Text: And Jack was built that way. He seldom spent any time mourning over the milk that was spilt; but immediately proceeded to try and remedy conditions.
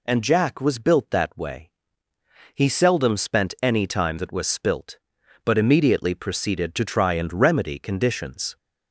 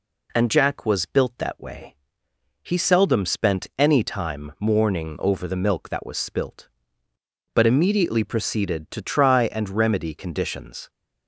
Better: second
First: skips "mourning over the milk"; at 4.1 s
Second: none

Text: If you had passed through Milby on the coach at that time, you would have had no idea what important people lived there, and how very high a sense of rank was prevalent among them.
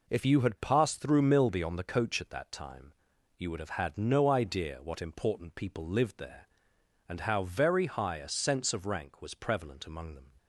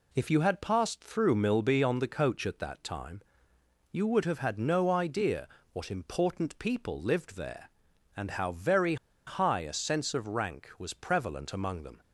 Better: first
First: none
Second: pauses between "idea" and "what"; slight; at 5.4 s; 0.24 s long // pauses between "very" and "high"; slight; at 8.9 s; 0.31 s long

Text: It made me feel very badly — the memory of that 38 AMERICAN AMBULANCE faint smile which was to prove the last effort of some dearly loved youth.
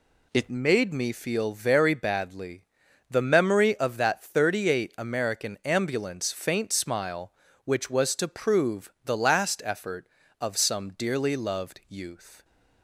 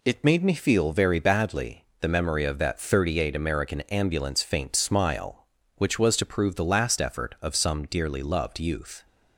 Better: second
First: changes voice at "made"; from 0.5 s on; 11.9 s long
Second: none

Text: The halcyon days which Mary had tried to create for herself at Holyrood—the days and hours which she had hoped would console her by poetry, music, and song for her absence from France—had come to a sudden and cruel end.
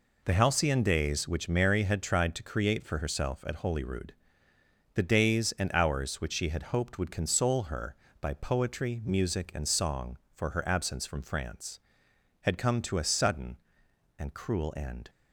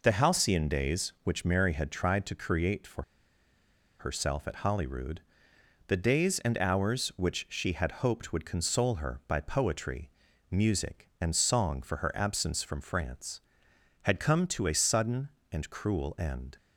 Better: first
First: none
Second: pauses between "for" and "herself"; noticeable; at 3.0 s; 0.96 s long

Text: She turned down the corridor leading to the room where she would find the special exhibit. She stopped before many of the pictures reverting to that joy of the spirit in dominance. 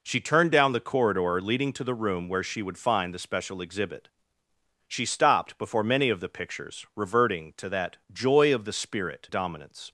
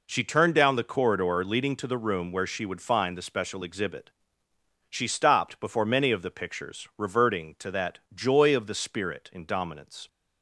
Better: second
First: skips "in"; at 9.2 s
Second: none

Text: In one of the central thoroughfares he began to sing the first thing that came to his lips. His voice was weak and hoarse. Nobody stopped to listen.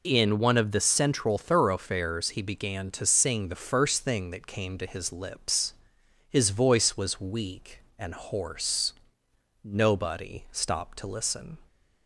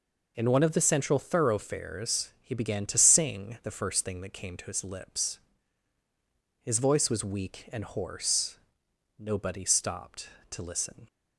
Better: neither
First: none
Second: none

